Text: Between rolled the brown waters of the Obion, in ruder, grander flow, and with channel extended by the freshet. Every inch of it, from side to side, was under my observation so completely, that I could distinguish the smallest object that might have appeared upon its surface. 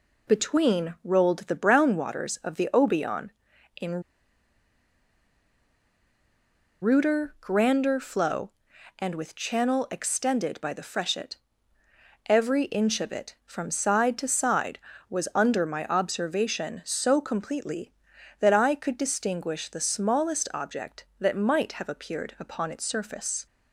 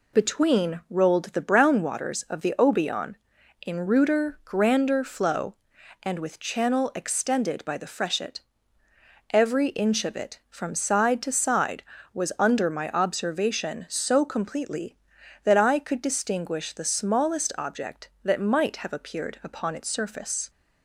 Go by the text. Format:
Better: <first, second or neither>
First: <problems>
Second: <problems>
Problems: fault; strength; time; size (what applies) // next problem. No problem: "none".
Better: second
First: pauses between "in" and "ruder"; strong; at 4.0 s; 2.7 s long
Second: none